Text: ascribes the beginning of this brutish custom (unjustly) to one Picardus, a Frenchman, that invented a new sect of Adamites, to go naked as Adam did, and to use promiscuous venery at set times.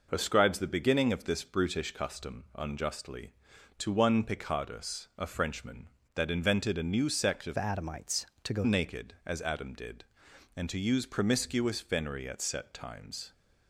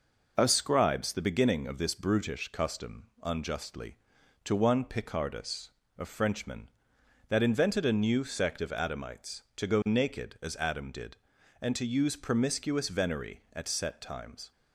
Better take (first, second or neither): second